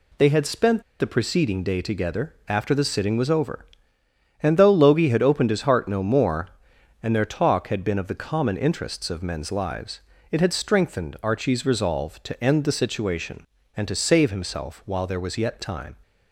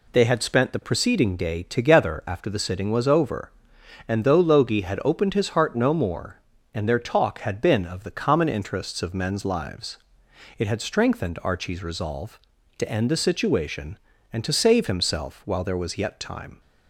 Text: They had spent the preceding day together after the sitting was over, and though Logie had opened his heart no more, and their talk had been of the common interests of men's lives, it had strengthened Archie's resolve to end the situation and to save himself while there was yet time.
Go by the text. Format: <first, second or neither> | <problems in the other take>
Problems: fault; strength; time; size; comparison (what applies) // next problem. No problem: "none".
second | pauses between "spent" and "the"; slight; at 0.8 s; 0.16 s long